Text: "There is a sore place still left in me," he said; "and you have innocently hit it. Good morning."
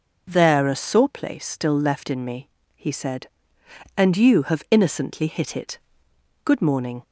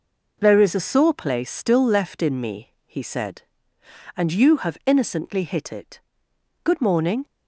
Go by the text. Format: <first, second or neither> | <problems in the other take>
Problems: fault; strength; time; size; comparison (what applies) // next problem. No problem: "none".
second | skips "is"; at 0.6 s